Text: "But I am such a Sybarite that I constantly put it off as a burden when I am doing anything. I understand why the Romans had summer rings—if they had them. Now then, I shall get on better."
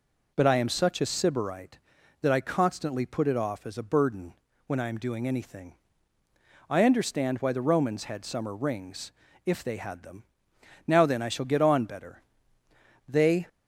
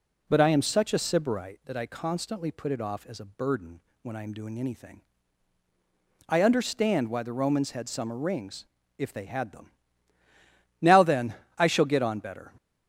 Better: second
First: pauses between "burden" and "when"; slight; at 4.3 s; 0.34 s long // goes on to say "They"; slight; from 13.0 s on; 0.40 s long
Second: pauses between "burden" and "when"; slight; at 3.7 s; 0.22 s long

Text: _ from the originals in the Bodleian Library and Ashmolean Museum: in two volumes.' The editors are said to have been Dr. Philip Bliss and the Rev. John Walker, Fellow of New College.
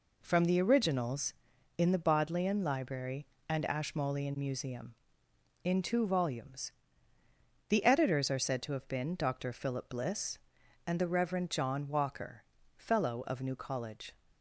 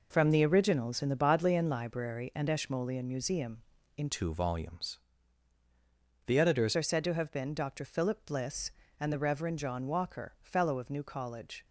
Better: first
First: none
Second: changes voice from "two" to "editors"; from 4.0 to 6.7 s; 2.7 s long

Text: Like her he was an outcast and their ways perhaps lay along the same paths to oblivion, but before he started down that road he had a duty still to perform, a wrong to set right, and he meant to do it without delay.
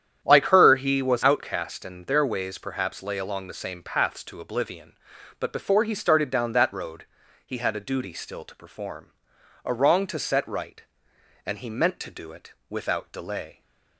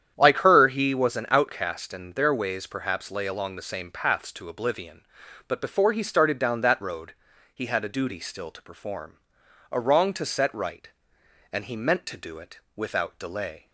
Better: second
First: starts louder than the rest; strong; until 1.2 s; 9.5 dB // skips "an"; at 1.2 s // pauses between "road" and "he"; at 7.0 s; 0.38 s long // pauses between "it" and "without"; slight; at 12.5 s; 0.18 s long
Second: starts louder than the rest; strong; until 1.1 s; 9 dB // pauses between "road" and "he"; at 7.1 s; 0.38 s long // pauses between "it" and "without"; slight; at 12.5 s; 0.18 s long

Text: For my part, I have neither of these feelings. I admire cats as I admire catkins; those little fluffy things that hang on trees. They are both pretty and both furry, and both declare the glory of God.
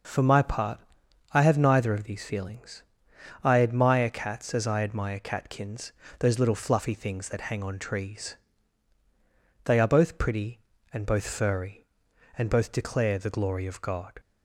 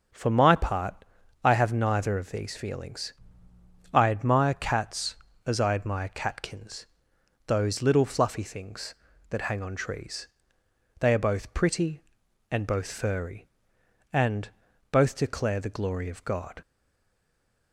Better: first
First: none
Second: pauses between "and" and "both"; at 14.4 s; 0.42 s long // stays silent after the last word; from 16.6 s on; 1.1 s long

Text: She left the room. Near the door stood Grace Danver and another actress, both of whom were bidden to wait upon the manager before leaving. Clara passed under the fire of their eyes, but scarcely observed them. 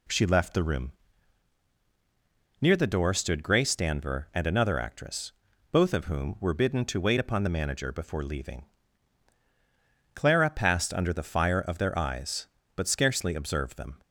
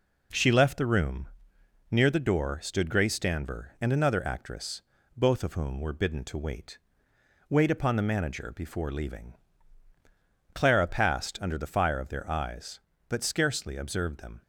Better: first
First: none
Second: says "wait" twice; at 7.4 s

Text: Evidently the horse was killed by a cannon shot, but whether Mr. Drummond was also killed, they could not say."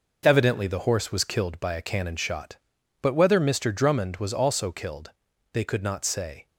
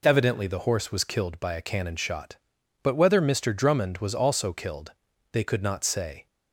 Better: second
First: gets quieter; strong; throughout; 7.5 dB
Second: none

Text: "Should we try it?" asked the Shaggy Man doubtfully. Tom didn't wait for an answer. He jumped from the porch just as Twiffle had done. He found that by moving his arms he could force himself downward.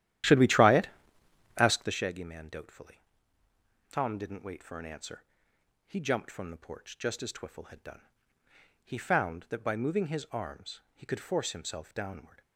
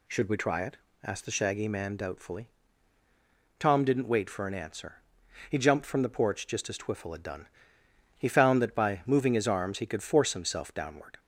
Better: second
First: starts louder than the rest; strong; until 2.1 s; 12 dB // pauses between "arms" and "he"; slight; at 10.7 s; 0.16 s long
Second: none

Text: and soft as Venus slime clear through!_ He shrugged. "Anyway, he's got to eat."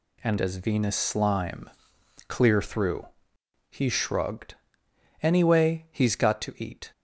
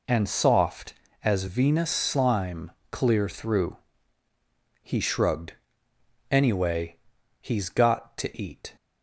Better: second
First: skips "soft"; at 0.3 s // pauses between "slime" and "clear"; noticeable; at 1.6 s; 0.58 s long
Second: pauses between "slime" and "clear"; slight; at 2.7 s; 0.20 s long

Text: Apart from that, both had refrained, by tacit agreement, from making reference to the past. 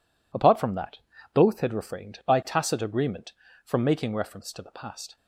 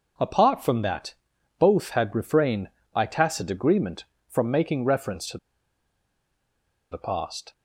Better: first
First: none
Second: pauses between "to" and "the"; strong; at 5.3 s; 1.5 s long

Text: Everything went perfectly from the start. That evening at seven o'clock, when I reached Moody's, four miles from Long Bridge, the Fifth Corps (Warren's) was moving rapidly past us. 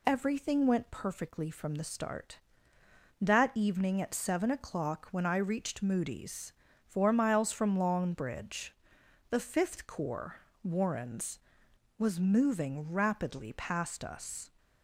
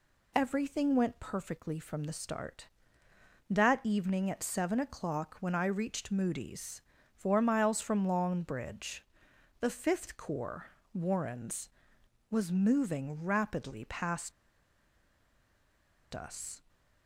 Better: first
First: none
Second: pauses between "past" and "us"; strong; at 14.3 s; 1.8 s long

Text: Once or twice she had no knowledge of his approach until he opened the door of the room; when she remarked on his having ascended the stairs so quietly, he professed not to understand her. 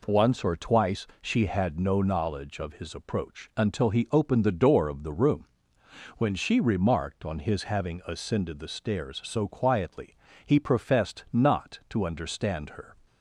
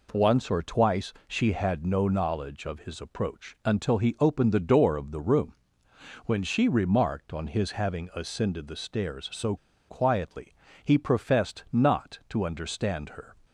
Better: first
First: none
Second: pauses between "so" and "quietly"; slight; at 9.5 s; 0.32 s long

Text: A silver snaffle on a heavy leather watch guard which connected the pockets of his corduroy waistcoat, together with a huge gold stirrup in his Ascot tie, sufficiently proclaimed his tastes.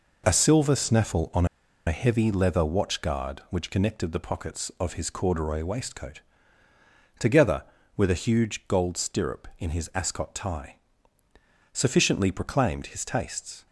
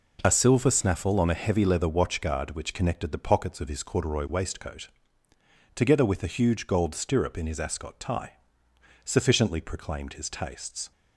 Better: second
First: pauses between "on" and "a"; at 1.4 s; 0.42 s long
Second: none

